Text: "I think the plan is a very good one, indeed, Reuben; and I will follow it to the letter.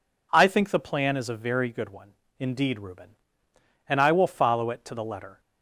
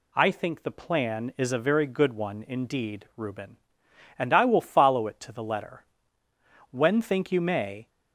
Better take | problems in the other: first | goes on to say "When think you may"; noticeable; from 6.7 s on; 1.1 s long

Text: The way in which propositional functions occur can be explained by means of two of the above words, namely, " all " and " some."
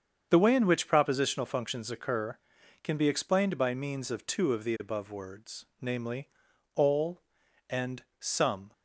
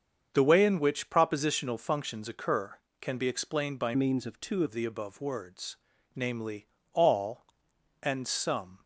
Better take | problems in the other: first | starts louder than the rest; strong; until 1.3 s; 7.5 dB; strong in the first // changes voice from "means" to "two"; from 3.9 to 4.6 s; 0.7 s long

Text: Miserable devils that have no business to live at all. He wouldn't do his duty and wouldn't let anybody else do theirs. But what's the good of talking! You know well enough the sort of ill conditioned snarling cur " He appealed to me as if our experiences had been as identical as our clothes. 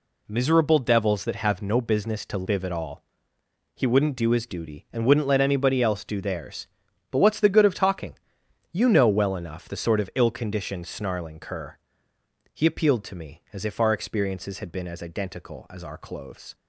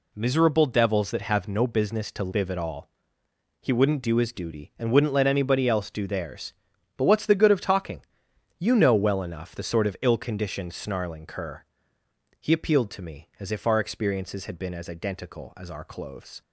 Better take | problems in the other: neither | none

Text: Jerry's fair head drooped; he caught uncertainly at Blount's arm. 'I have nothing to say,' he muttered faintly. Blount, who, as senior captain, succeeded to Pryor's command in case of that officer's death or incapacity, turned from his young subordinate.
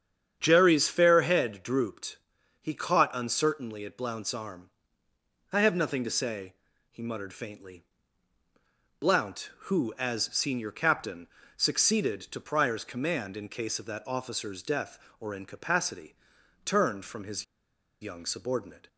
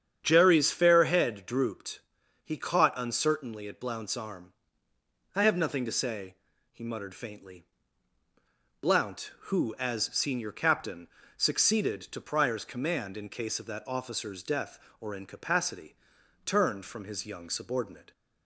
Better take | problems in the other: second | starts louder than the rest; strong; until 1.4 s; 8.5 dB; strong in the second // pauses between "his" and "young"; noticeable; at 17.4 s; 0.58 s long

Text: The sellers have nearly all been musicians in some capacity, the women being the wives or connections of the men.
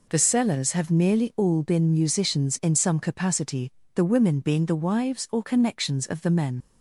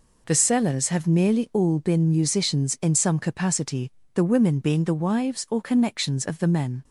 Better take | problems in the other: second | leaves "men" unfinished; at 6.6 s; 60 ms

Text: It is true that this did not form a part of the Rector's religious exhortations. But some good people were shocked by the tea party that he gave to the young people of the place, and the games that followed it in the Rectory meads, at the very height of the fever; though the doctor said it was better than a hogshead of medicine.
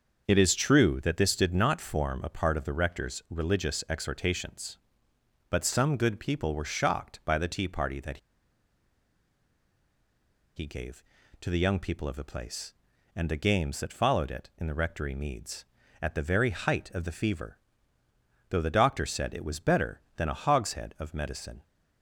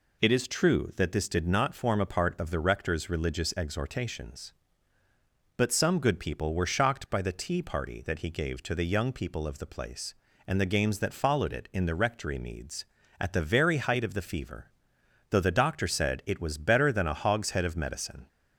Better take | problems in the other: second | starts louder than the rest; until 1.3 s; 6 dB // pauses between "that" and "he"; strong; at 8.1 s; 2.3 s long

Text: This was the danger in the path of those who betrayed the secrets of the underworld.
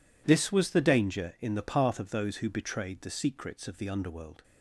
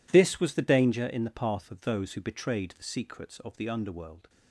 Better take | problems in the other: neither | none

